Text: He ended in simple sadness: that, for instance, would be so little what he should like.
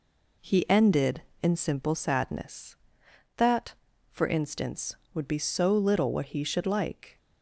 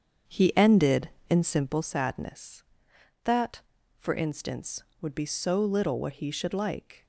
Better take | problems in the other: first | starts louder than the rest; strong; until 1.9 s; 7.5 dB

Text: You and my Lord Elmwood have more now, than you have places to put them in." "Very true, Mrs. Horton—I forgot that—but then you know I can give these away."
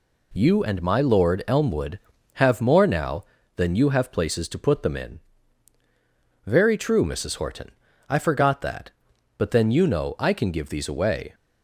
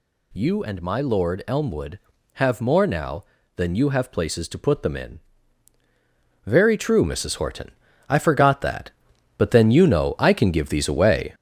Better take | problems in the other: first | gets louder; noticeable; throughout; 5.5 dB

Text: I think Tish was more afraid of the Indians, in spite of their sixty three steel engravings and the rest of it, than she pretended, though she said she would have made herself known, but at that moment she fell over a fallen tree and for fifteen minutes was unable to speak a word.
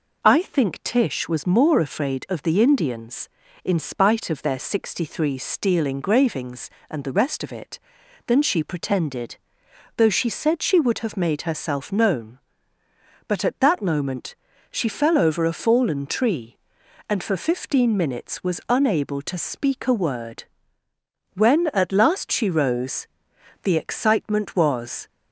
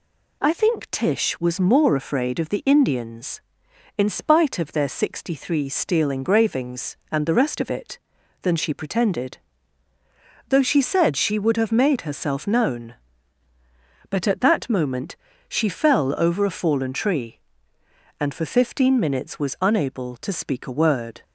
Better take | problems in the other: second | pauses between "moment" and "she"; slight; at 14.3 s; 0.36 s long; slight in the second // goes on to say "When at last she rose the excitement was"; strong; from 21.3 s on; 3.7 s long

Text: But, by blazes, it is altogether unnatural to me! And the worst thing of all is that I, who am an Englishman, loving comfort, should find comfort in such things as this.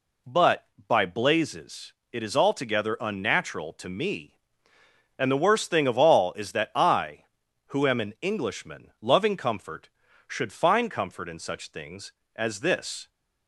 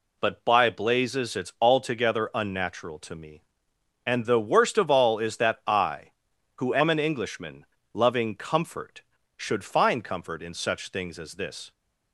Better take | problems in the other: first | skips "thing"; at 4.7 s

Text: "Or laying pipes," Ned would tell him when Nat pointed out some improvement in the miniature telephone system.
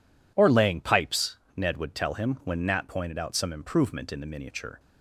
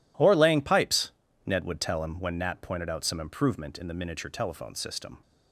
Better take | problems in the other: second | stops before "telephone system"; at 4.7 s

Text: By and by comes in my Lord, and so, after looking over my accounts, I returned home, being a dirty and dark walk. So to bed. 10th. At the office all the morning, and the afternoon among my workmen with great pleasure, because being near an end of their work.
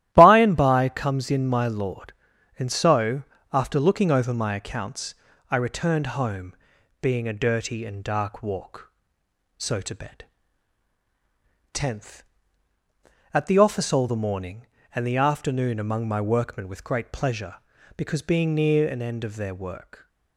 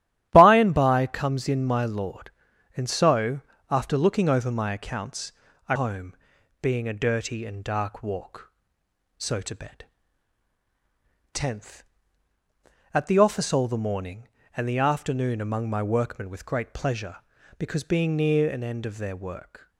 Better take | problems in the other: first | starts louder than the rest; strong; until 1.3 s; 13 dB; strong in the first // skips "returned"; at 5.7 s

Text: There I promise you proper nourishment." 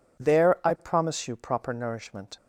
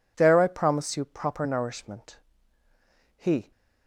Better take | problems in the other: first | goes on to say "He"; slight; from 3.1 s on; 0.34 s long

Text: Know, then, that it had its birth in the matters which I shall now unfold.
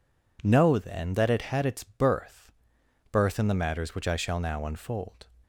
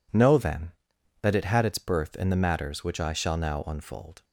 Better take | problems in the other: second | says "birth" twice; at 3.1 s

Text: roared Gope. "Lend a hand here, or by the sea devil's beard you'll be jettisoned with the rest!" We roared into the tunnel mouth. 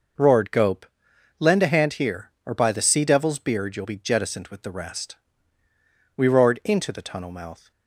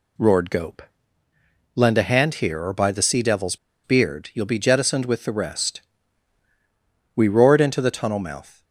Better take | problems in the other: first | pauses between "devil's" and "beard"; slight; at 3.5 s; 0.28 s long

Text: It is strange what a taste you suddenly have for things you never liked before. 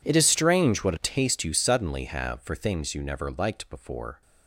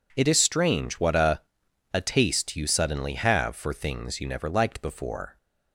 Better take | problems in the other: first | says "a" twice; at 1.9 s

